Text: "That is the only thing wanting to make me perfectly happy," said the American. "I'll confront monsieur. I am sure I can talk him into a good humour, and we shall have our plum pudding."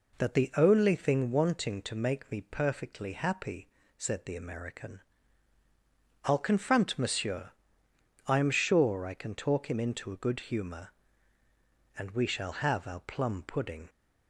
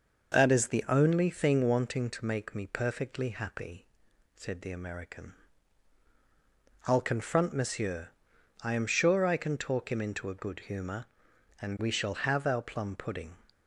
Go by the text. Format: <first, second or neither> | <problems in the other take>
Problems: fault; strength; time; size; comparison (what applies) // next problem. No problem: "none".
second | skips "is"; at 0.3 s